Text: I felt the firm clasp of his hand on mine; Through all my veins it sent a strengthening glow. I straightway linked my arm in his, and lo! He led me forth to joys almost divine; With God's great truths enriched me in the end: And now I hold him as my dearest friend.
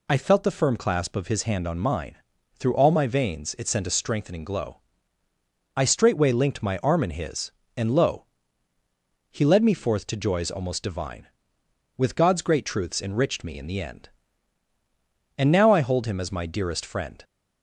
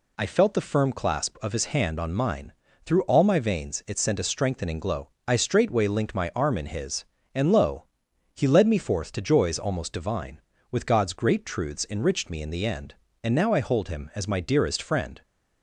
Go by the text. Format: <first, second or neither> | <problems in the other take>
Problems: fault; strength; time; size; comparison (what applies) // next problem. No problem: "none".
neither | none